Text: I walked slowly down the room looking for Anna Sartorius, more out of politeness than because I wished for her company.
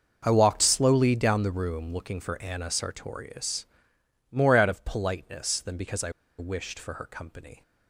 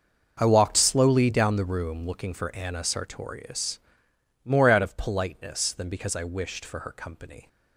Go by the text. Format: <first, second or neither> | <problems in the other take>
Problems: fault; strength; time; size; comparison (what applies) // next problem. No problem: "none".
second | starts louder than the rest; until 1.2 s; 6 dB; also in the second // pauses between "I" and "wished"; slight; at 6.1 s; 0.27 s long